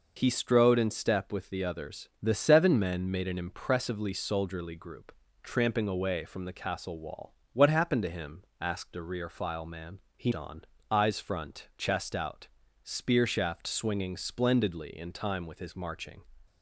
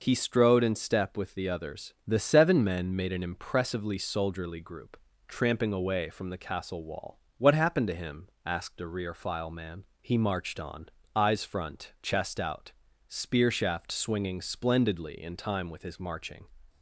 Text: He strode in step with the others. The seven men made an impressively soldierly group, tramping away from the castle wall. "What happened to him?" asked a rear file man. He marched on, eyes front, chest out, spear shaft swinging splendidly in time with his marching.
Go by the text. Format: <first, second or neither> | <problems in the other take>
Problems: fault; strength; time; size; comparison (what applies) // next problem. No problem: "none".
second | skips "marched"; at 10.3 s